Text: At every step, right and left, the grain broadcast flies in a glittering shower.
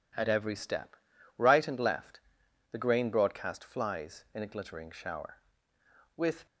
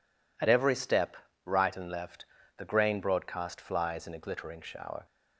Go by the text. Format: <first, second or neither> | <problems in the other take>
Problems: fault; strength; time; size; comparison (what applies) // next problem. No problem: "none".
second | goes on to say "With"; slight; from 6.1 s on; 0.30 s long